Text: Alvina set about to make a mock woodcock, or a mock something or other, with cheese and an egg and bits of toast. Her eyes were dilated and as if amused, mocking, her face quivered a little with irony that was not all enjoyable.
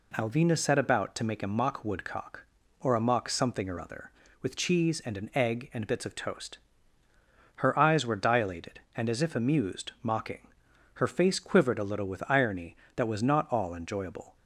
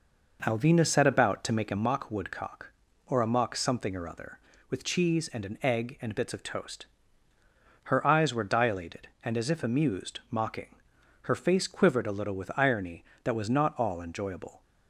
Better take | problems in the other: first | starts louder than the rest; noticeable; until 1.9 s; 5 dB

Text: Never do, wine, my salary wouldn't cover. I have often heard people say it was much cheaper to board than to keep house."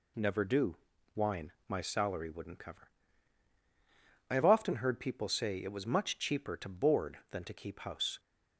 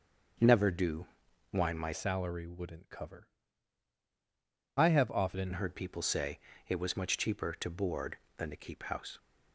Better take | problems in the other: first | starts louder than the rest; until 1.8 s; 6.5 dB // changes voice from "salary" to "often"; from 1.9 to 5.5 s; 3.6 s long // pauses between "say" and "it"; slight; at 6.3 s; 0.30 s long

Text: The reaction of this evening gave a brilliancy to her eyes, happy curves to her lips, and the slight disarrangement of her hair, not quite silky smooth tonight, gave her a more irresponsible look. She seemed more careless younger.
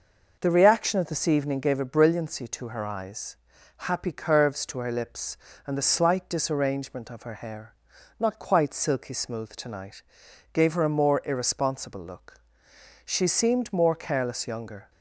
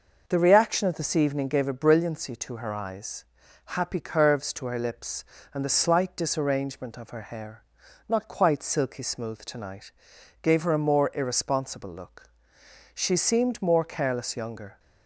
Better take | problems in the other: neither | none

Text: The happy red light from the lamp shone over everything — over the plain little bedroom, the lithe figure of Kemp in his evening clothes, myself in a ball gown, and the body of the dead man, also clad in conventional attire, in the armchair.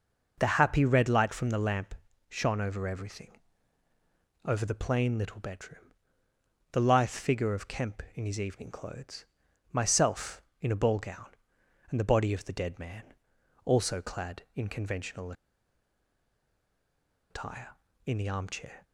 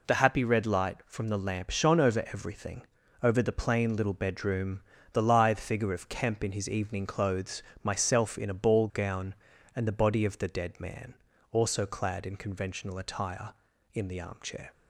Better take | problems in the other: second | pauses between "lamp" and "shone"; slight; at 1.9 s; 0.34 s long // pauses between "conventional" and "attire"; strong; at 15.3 s; 1.9 s long

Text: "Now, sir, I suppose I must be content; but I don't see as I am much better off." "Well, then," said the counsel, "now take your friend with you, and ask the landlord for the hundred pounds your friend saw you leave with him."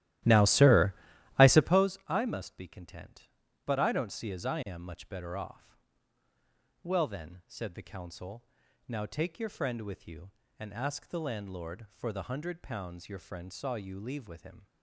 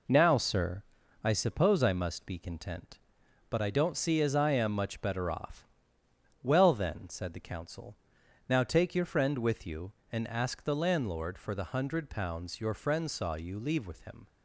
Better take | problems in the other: second | starts louder than the rest; strong; until 1.9 s; 14 dB

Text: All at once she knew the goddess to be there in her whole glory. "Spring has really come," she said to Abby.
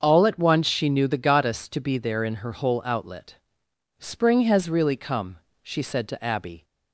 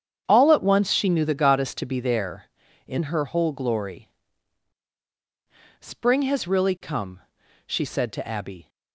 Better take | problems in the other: second | starts louder than the rest; until 1.0 s; 6.5 dB; strong in the second // says "outlet" for "glory"; at 2.8 s

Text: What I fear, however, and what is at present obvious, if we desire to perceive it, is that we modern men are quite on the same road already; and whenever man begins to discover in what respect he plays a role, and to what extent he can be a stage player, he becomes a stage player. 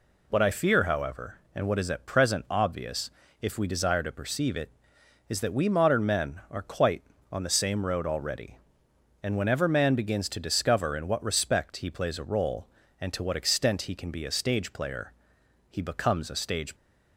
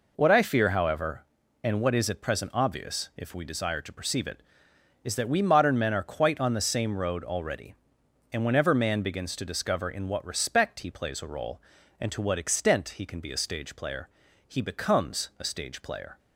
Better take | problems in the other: second | stops before "player"; at 16.7 s

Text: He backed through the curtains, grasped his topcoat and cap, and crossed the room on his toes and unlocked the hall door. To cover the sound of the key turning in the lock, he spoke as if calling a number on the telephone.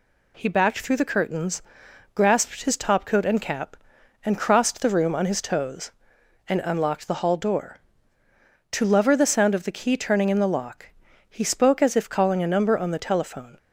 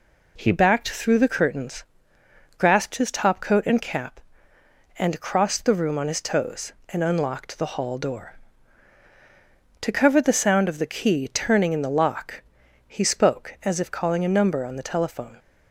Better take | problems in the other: second | says "lover" for "cover"; at 8.8 s

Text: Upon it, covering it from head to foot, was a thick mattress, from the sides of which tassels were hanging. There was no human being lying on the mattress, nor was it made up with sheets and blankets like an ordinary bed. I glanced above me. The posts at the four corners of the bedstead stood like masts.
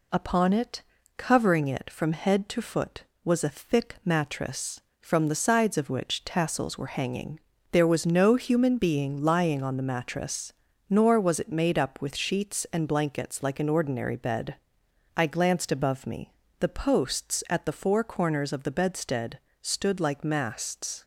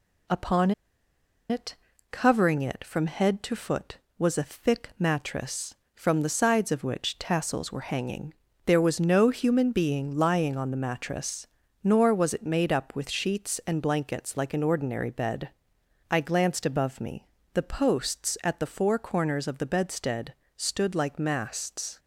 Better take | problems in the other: first | pauses between "Upon" and "it"; noticeable; at 0.7 s; 0.78 s long // pauses between "bedstead" and "stood"; slight; at 20.3 s; 0.24 s long; slight in the first

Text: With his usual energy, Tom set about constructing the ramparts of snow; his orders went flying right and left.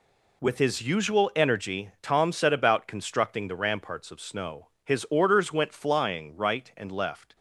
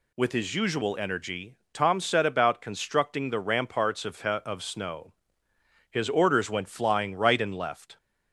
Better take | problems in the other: first | says "of" twice; at 4.2 s

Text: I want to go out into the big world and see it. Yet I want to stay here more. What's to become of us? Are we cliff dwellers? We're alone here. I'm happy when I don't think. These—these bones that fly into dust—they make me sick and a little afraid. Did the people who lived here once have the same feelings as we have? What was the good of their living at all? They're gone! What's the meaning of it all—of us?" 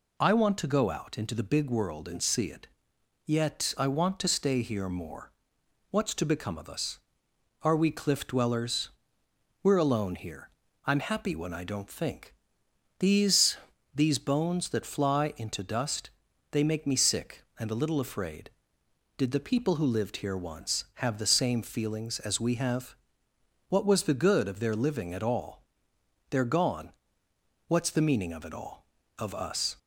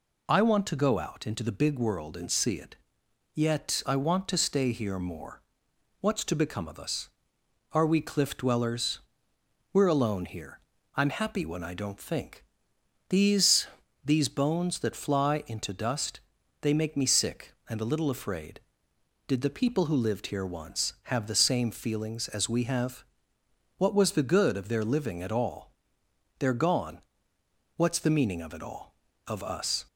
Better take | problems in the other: neither | none

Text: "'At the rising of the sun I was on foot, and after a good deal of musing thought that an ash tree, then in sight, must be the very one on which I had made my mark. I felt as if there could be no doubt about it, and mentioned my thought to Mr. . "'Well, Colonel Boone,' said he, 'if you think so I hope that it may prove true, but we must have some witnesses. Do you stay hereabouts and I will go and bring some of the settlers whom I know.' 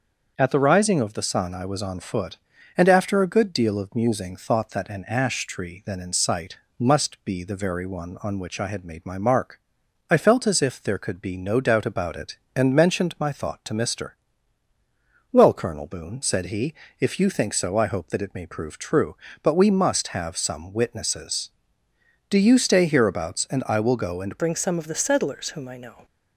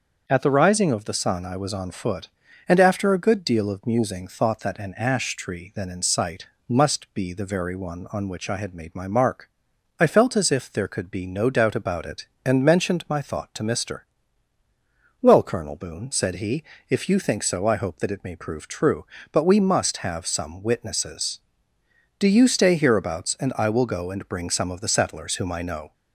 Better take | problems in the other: second | starts louder than the rest; until 1.3 s; 6.5 dB; also in the second // changes voice at "bring"; from 24.3 s on; 1.7 s long

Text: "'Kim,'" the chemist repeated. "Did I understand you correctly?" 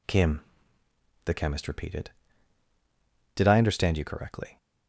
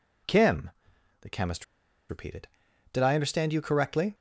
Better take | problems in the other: first | pauses between "chemist" and "repeated"; at 1.6 s; 0.45 s long

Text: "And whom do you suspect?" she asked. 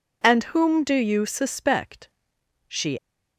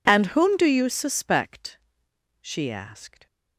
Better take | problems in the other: second | stops before "asked"; at 2.9 s

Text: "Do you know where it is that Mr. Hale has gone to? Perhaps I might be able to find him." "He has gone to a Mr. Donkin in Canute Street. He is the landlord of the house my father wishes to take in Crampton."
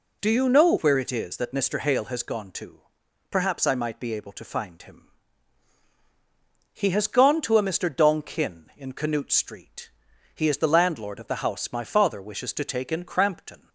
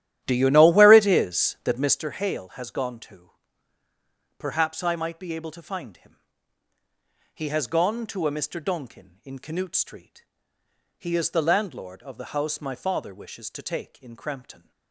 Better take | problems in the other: first | starts louder than the rest; strong; until 2.0 s; 11.5 dB

